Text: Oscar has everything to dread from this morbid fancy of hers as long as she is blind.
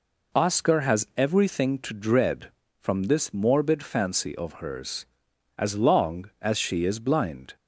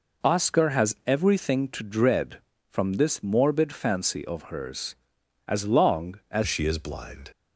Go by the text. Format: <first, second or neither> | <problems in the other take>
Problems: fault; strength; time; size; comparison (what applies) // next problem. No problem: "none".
first | changes voice at "she"; from 6.4 s on; 0.9 s long